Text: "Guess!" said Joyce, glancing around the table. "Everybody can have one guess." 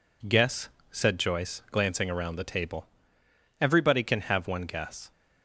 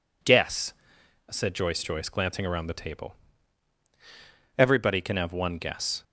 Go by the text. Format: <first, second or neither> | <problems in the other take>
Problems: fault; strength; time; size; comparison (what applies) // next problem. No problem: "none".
first | says "Joyce" twice; at 1.8 s